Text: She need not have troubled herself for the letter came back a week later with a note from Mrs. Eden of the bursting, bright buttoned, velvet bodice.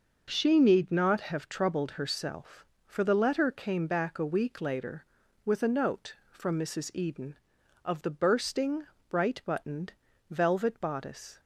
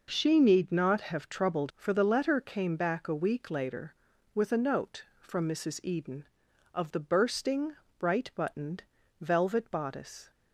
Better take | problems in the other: first | skips "herself"; at 1.7 s

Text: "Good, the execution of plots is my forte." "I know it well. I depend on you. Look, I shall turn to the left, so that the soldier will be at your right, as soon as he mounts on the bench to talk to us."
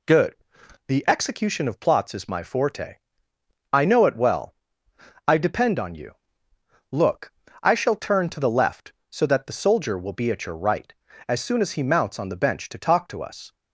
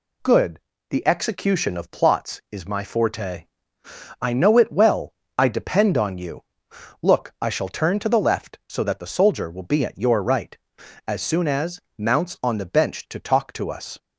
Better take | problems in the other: first | skips "he"; at 11.8 s

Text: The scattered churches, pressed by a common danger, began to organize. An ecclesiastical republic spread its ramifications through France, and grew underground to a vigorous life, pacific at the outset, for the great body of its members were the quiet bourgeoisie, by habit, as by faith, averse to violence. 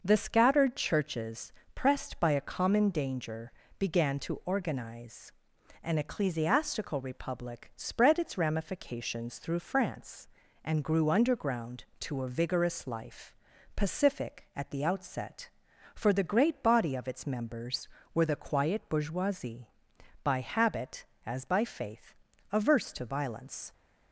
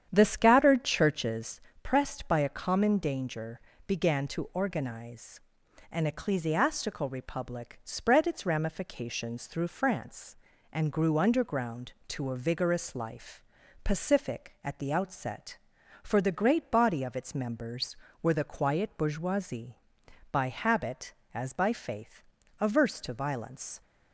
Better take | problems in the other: first | starts louder than the rest; strong; until 1.6 s; 9 dB

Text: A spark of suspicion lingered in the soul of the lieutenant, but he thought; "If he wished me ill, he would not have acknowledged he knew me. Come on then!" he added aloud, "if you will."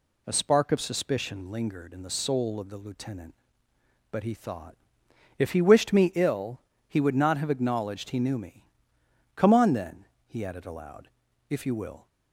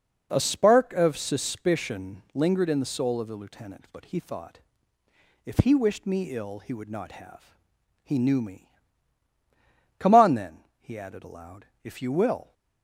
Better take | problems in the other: first | skips "acknowledged"; at 7.8 s

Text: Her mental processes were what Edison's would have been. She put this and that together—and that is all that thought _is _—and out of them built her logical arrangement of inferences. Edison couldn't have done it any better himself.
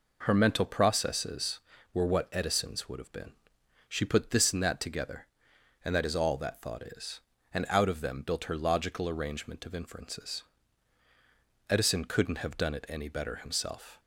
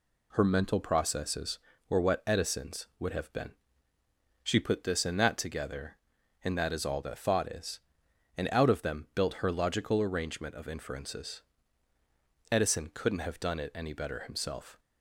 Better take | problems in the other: neither | none

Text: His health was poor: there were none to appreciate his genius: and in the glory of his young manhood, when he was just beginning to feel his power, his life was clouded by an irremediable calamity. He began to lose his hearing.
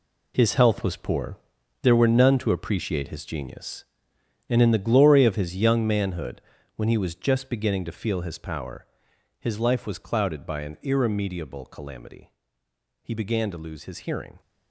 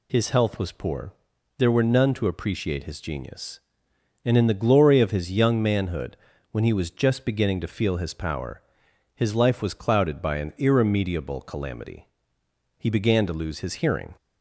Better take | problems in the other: second | gets quieter; strong; throughout; 11 dB

